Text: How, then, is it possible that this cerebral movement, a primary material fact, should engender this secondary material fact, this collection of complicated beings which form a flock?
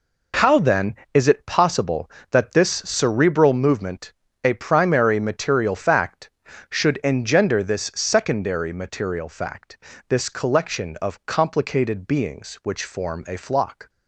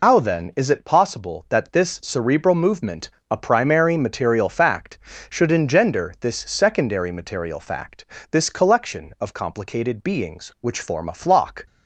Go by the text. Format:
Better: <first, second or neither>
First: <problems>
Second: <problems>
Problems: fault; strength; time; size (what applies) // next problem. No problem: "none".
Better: first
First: none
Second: loses the start of "How"; at 0.0 s; 110 ms